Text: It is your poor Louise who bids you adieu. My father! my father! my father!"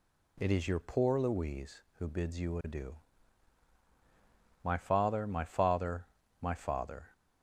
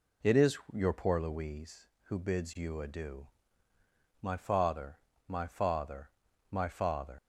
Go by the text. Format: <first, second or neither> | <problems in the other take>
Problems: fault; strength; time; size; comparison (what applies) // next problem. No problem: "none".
first | pauses between "is" and "your"; slight; at 0.5 s; 0.16 s long // leaves "father" unfinished; at 7.1 s; 95 ms